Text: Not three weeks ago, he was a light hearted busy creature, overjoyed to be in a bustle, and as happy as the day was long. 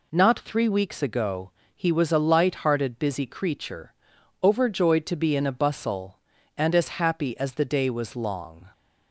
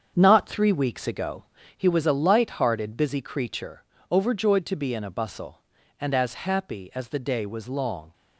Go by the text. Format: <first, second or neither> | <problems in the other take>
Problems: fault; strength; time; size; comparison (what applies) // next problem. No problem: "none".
first | gets quieter; strong; throughout; 8 dB